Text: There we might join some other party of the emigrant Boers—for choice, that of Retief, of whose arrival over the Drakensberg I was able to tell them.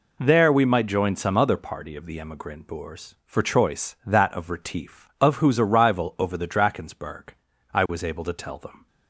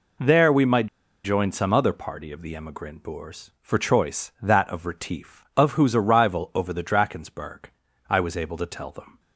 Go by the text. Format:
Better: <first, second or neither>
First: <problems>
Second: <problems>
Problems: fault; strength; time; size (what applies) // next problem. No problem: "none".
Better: first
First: pauses between "Drakensberg" and "I"; at 7.2 s; 0.44 s long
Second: pauses between "might" and "join"; at 0.8 s; 0.38 s long // pauses between "Drakensberg" and "I"; at 7.6 s; 0.44 s long